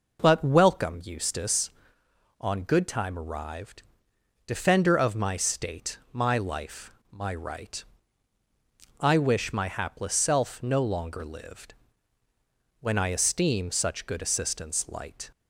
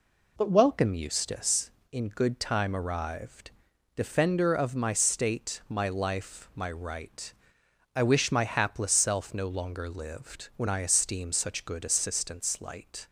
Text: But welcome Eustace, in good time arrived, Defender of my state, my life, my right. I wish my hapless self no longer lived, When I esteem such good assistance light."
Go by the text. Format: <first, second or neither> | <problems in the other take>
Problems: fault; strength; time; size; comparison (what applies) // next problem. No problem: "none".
second | says "on" for "in"; at 2.3 s